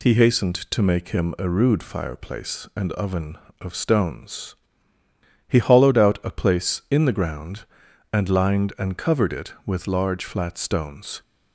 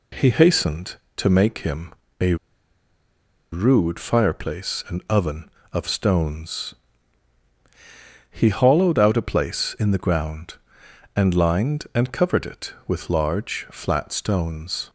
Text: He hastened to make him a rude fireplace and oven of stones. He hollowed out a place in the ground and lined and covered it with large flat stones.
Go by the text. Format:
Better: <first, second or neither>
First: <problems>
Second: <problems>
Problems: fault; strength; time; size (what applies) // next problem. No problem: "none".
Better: first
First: none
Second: pauses between "him" and "a"; slight; at 1.9 s; 0.28 s long // pauses between "a" and "rude"; at 2.3 s; 1.1 s long